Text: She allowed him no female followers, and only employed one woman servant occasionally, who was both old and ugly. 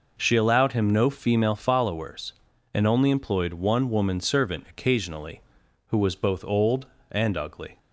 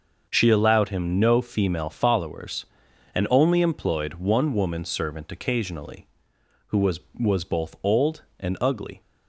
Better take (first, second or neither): first